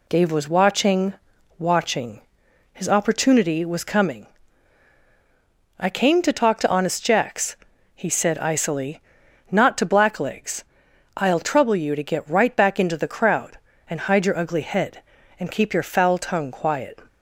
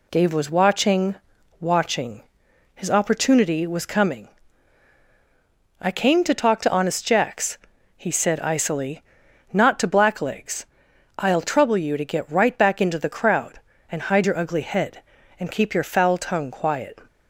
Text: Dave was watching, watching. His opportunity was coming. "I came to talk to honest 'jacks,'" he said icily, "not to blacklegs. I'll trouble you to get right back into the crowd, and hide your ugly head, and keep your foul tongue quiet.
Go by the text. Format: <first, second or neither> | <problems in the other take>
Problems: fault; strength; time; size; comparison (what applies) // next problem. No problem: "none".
neither | none